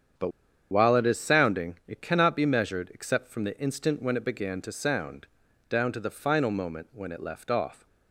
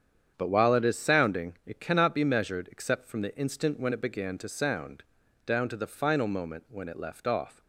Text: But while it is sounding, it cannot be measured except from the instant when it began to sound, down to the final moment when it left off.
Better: second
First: starts louder than the rest; strong; until 1.5 s; 8 dB // pauses between "But" and "while"; at 0.3 s; 0.40 s long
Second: starts louder than the rest; strong; until 1.3 s; 8 dB

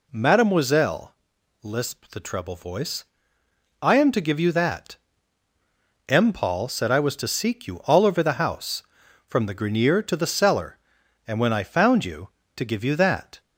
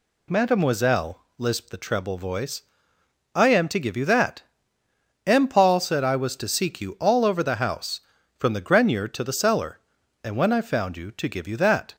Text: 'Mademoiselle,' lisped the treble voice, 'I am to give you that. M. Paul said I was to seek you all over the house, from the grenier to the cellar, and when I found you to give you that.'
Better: neither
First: none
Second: none

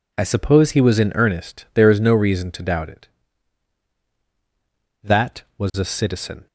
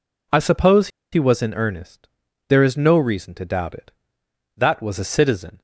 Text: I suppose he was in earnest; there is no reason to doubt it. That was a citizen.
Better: first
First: none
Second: pauses between "suppose" and "he"; slight; at 0.8 s; 0.24 s long

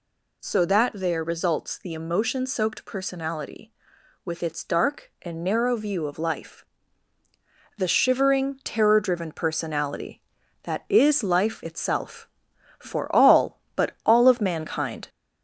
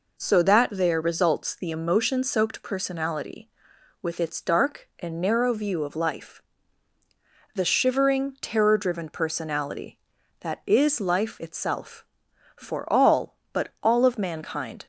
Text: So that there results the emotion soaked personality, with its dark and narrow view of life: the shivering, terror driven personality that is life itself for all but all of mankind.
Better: second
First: gets louder; slight; throughout; 2.5 dB // pauses between "but" and "all"; slight; at 13.9 s; 0.16 s long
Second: pauses between "but" and "all"; slight; at 13.6 s; 0.16 s long

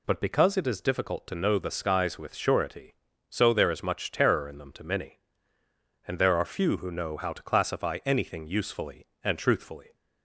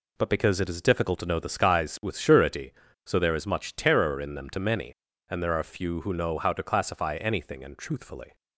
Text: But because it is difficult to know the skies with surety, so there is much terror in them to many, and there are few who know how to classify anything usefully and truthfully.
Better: first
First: none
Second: skips "usefully"; at 7.6 s

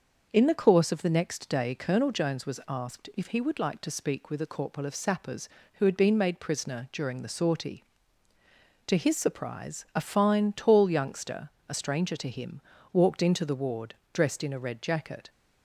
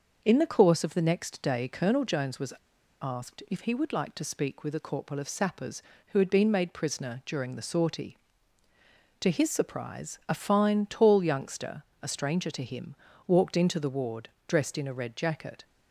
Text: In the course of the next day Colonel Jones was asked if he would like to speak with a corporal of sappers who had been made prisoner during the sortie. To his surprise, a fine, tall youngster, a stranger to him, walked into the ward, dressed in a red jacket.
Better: first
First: starts louder than the rest; until 1.3 s; 6.5 dB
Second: starts louder than the rest; until 1.2 s; 6.5 dB // pauses between "was" and "asked"; noticeable; at 2.5 s; 0.48 s long

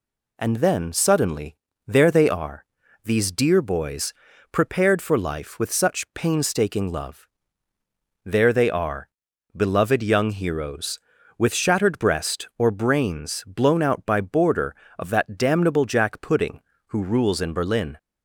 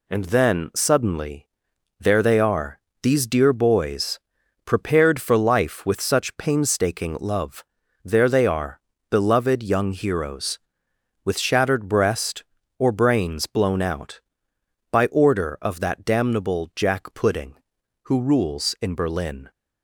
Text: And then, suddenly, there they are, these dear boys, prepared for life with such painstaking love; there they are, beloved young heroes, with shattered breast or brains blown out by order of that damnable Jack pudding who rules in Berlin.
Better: second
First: says "border" for "order"; at 14.2 s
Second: none

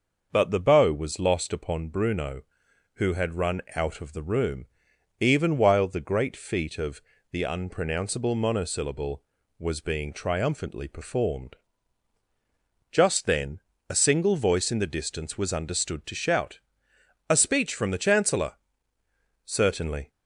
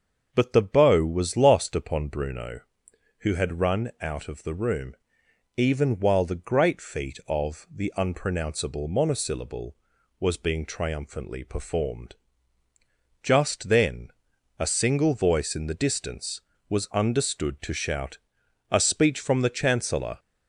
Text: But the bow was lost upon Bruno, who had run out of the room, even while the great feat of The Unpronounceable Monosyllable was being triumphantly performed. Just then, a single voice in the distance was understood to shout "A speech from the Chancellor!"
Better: second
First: starts louder than the rest; until 1.3 s; 6 dB // pauses between "of" and "The"; slight; at 6.9 s; 0.32 s long // pauses between "shout" and "A"; noticeable; at 16.5 s; 0.70 s long // goes on to say "Certainly"; noticeable; from 19.4 s on; 0.64 s long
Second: starts louder than the rest; until 1.3 s; 6.5 dB // pauses between "shout" and "A"; noticeable; at 18.1 s; 0.52 s long

